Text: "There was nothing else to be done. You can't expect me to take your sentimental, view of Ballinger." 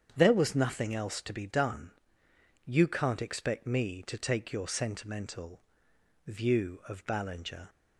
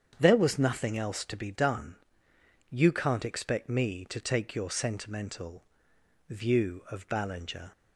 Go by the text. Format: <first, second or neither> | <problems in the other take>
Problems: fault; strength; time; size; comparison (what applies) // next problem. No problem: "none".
neither | starts louder than the rest; strong; the same in both